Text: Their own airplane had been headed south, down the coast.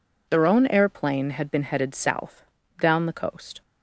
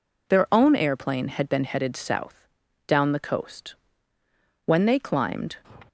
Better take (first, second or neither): first